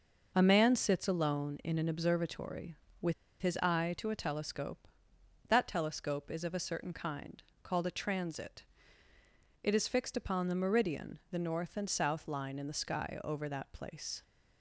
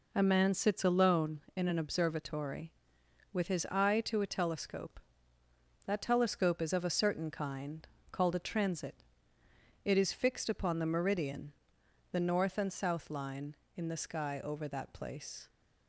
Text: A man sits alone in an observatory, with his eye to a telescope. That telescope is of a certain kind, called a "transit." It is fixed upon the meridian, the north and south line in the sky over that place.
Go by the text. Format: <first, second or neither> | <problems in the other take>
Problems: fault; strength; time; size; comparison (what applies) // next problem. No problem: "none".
second | pauses between "with" and "his"; slight; at 3.1 s; 0.28 s long